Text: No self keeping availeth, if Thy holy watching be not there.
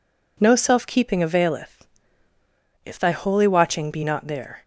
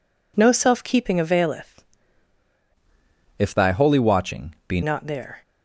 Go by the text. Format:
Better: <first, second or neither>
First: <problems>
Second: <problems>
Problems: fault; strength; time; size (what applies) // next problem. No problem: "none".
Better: first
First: none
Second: changes voice from "if" to "be"; from 3.3 to 4.8 s; 1.5 s long